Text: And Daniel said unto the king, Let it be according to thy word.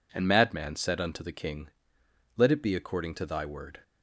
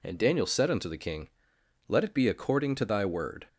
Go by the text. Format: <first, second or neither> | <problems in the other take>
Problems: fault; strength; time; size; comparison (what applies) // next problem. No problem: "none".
second | says "Madman" for "Daniel"; at 0.2 s